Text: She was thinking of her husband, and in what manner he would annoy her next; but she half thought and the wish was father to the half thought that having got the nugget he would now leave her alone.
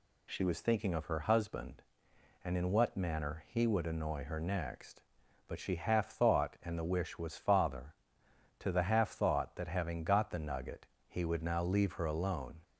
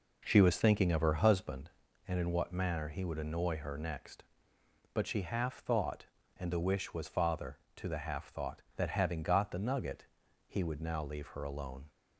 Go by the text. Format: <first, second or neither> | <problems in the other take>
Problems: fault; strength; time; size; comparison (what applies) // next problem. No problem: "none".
first | starts louder than the rest; noticeable; until 1.5 s; 5.5 dB // pauses between "nugget" and "he"; at 10.0 s; 0.42 s long; slight in the first